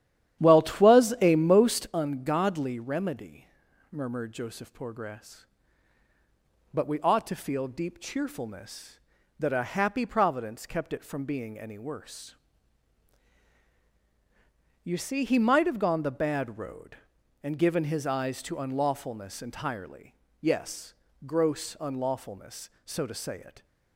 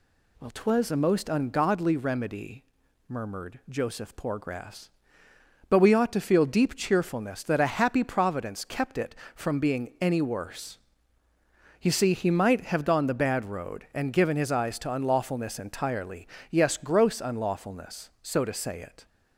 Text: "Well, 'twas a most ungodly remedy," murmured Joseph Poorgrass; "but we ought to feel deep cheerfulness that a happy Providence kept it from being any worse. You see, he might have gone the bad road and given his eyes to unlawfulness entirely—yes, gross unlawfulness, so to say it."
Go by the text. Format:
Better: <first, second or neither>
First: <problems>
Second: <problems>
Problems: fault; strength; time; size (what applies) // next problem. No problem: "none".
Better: second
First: starts louder than the rest; strong; until 1.9 s; 11 dB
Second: none